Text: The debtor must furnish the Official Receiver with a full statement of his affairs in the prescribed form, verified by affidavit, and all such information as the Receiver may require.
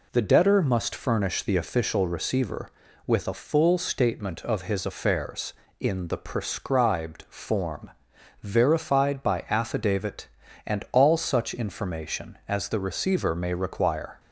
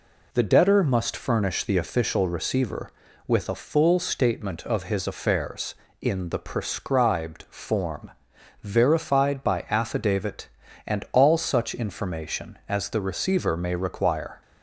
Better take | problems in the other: neither | none

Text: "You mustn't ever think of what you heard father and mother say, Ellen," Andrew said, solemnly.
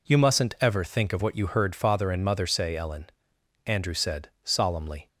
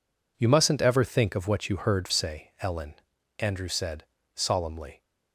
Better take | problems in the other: first | skips "father and mother"; at 2.0 s

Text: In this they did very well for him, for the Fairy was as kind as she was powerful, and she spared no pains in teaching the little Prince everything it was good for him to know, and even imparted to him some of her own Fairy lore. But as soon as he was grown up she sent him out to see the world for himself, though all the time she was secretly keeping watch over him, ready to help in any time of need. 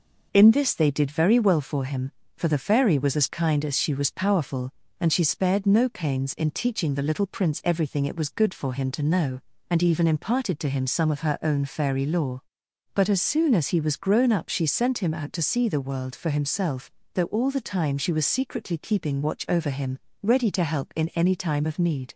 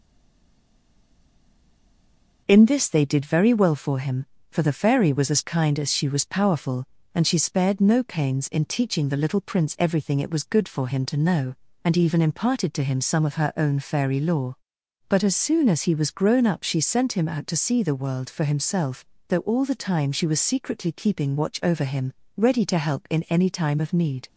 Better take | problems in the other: first | stays silent before the first word; until 2.4 s; 2.4 s long

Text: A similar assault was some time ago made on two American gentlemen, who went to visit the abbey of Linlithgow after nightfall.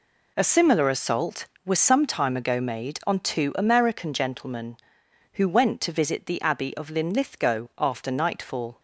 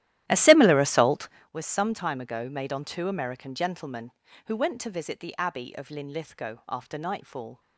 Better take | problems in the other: first | starts louder than the rest; strong; until 1.5 s; 13.5 dB

